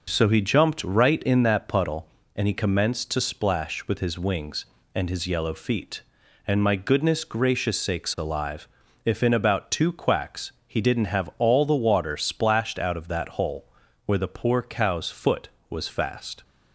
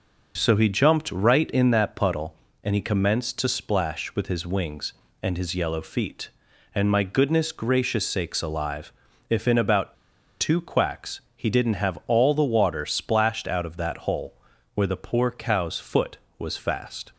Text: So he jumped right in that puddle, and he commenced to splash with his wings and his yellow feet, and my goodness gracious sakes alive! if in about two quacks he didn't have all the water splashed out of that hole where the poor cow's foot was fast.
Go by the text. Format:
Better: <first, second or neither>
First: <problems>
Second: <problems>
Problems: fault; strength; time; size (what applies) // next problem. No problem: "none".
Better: first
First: pauses between "quacks" and "he"; slight; at 10.5 s; 0.16 s long // pauses between "hole" and "where"; slight; at 13.7 s; 0.32 s long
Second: pauses between "about" and "two"; noticeable; at 9.9 s; 0.46 s long // pauses between "quacks" and "he"; slight; at 11.2 s; 0.16 s long // pauses between "hole" and "where"; slight; at 14.4 s; 0.32 s long